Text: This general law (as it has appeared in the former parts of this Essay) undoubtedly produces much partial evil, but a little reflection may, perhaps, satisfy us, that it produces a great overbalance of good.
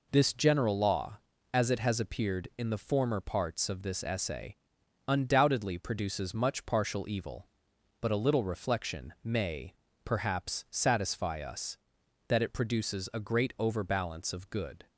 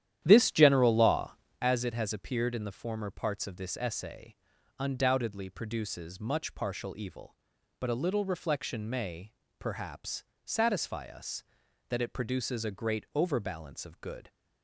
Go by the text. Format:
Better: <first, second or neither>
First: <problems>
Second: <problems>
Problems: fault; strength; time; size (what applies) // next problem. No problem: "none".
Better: first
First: none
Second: starts louder than the rest; strong; until 1.6 s; 11 dB